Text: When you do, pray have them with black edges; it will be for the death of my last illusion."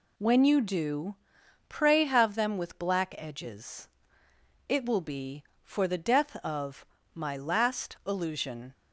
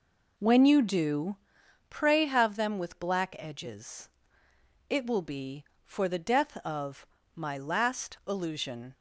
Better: first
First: pauses between "of" and "my"; slight; at 6.8 s; 0.28 s long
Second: starts louder than the rest; noticeable; until 1.5 s; 4.5 dB // pauses between "of" and "my"; slight; at 7.0 s; 0.28 s long

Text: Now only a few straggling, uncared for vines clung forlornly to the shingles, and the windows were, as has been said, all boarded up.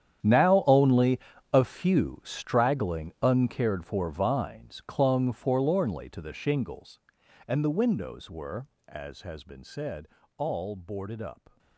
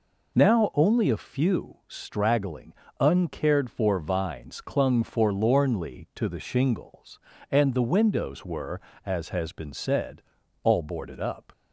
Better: second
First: gets quieter; strong; throughout; 16.5 dB // pauses between "only" and "a"; slight; at 1.2 s; 0.32 s long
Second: none

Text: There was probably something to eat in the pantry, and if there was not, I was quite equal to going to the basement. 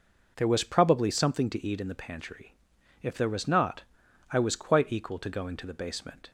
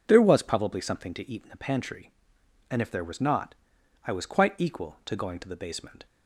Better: second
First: skips "and"; at 2.7 s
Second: none

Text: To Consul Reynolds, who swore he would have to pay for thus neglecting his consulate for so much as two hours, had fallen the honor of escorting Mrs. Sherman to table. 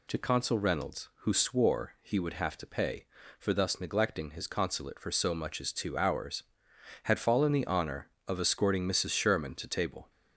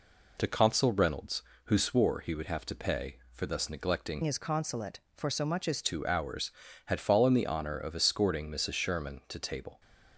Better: first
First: none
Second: changes voice from "his" to "as"; from 4.2 to 5.8 s; 1.6 s long

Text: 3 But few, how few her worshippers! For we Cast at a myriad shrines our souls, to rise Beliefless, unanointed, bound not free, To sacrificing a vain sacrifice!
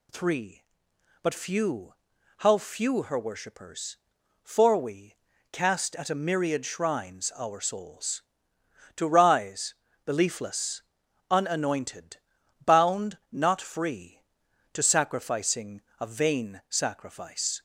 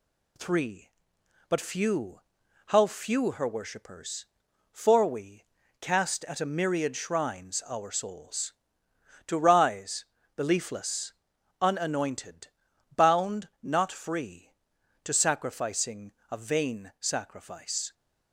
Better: first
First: pauses between "we" and "Cast"; at 5.1 s; 0.38 s long // pauses between "rise" and "Beliefless"; slight; at 9.7 s; 0.32 s long // pauses between "sacrificing" and "a"; slight; at 15.8 s; 0.18 s long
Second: gets quieter; slight; throughout; 2 dB // pauses between "we" and "Cast"; at 5.4 s; 0.38 s long // pauses between "rise" and "Beliefless"; slight; at 10.0 s; 0.32 s long // pauses between "sacrificing" and "a"; slight; at 16.1 s; 0.18 s long

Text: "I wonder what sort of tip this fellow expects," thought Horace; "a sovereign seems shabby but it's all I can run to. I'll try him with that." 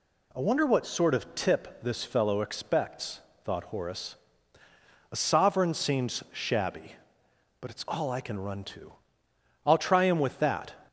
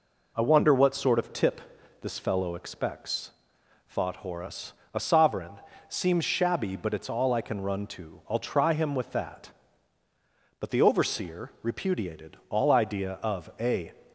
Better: first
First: none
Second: pauses between "tip" and "this"; at 1.6 s; 0.40 s long // pauses between "sovereign" and "seems"; slight; at 5.6 s; 0.26 s long // goes on to say "But the overseer repudiated all idea of a"; strong; from 10.5 s on; 3.3 s long

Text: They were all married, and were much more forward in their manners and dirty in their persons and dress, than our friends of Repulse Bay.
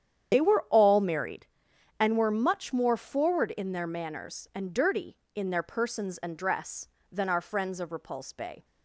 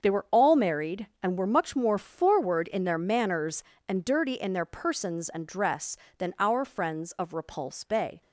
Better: second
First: loses the start of "They"; at 0.3 s; 75 ms // starts louder than the rest; strong; until 1.3 s; 9 dB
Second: starts louder than the rest; until 1.0 s; 7 dB

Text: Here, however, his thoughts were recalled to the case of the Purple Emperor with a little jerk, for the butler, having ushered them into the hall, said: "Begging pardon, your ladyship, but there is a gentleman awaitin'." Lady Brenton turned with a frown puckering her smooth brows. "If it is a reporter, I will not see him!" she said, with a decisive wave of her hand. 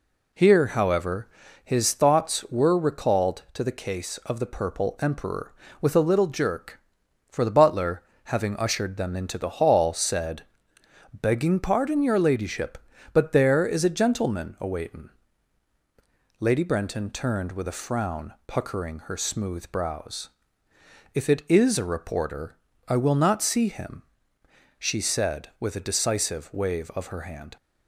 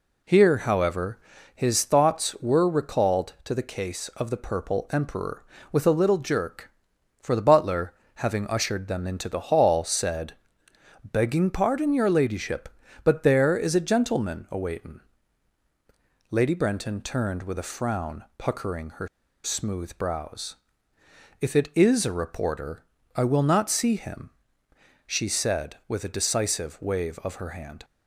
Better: first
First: none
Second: pauses between "her" and "smooth"; at 19.0 s; 0.36 s long

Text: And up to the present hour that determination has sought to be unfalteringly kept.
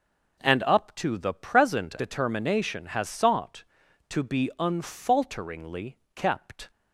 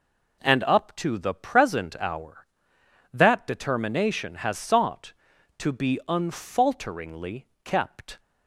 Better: second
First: skips "hour that"; at 1.9 s // pauses between "unfalteringly" and "kept"; slight; at 5.9 s; 0.16 s long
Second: pauses between "unfalteringly" and "kept"; slight; at 7.4 s; 0.16 s long

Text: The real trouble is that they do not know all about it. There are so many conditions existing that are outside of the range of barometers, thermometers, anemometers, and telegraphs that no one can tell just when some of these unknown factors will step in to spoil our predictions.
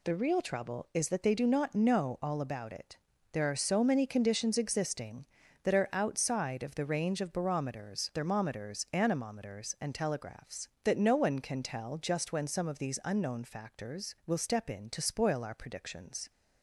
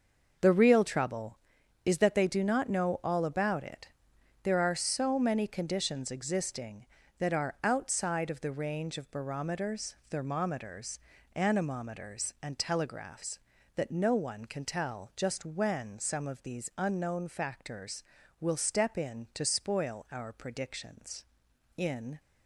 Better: first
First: none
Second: starts louder than the rest; noticeable; until 1.8 s; 6 dB // goes on to say "In"; slight; from 21.7 s on; 0.44 s long

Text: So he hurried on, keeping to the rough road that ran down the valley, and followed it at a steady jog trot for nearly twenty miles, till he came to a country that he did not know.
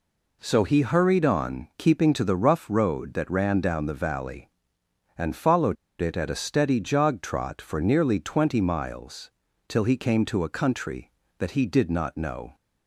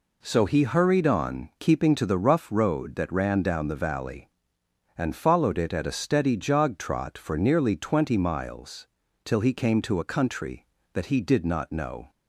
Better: second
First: pauses between "followed" and "it"; slight; at 5.7 s; 0.25 s long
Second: none

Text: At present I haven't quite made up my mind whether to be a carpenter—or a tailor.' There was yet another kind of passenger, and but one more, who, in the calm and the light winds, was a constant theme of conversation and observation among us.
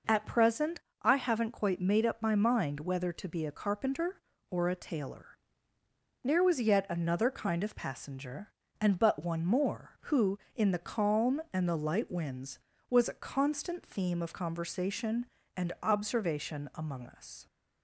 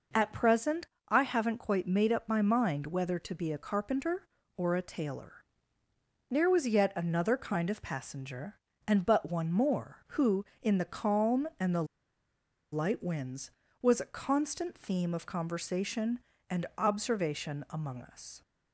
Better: first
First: pauses between "present" and "I"; slight; at 0.7 s; 0.22 s long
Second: pauses between "present" and "I"; slight; at 0.8 s; 0.22 s long // pauses between "the" and "light"; noticeable; at 11.8 s; 0.88 s long

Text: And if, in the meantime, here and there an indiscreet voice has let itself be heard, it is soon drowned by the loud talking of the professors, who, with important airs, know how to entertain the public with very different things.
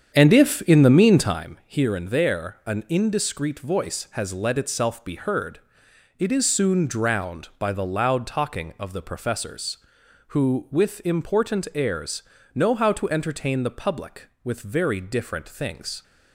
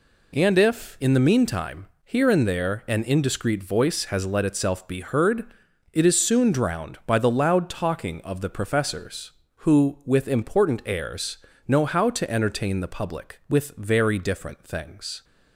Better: second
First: starts louder than the rest; strong; until 1.6 s; 8 dB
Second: none

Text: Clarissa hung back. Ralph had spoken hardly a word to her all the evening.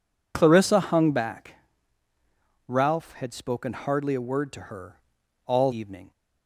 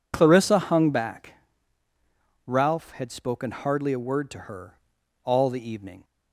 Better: second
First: pauses between "her" and "all"; noticeable; at 4.9 s; 0.46 s long // skips "the"; at 5.7 s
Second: pauses between "her" and "all"; noticeable; at 4.7 s; 0.46 s long

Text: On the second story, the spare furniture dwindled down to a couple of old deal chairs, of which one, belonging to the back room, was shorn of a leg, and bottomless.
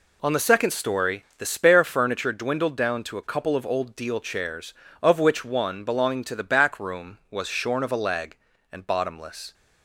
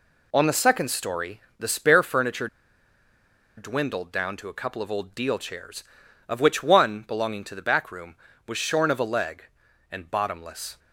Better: first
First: none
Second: pauses between "furniture" and "dwindled"; at 2.4 s; 1.1 s long

